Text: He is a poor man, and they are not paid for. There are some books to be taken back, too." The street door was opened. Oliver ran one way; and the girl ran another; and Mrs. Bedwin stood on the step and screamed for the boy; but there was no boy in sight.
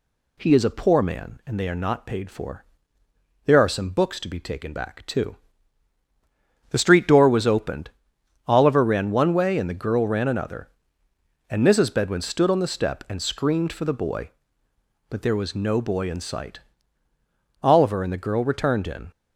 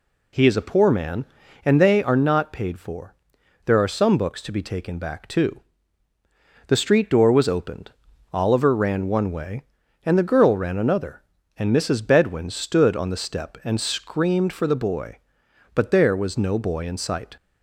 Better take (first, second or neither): second